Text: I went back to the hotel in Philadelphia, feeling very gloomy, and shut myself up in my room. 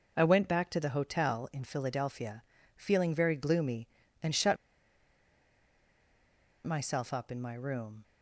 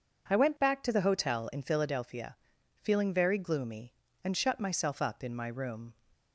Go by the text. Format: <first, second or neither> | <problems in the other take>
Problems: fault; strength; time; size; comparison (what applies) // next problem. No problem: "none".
second | pauses between "shut" and "myself"; strong; at 4.5 s; 2.1 s long